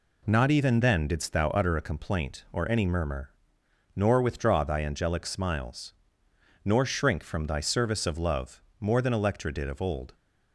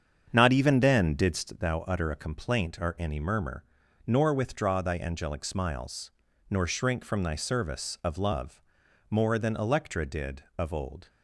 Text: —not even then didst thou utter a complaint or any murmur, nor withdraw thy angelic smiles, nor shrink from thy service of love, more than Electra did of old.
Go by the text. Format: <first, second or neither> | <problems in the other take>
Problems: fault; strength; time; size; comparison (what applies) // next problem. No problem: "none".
first | starts louder than the rest; strong; until 1.7 s; 7.5 dB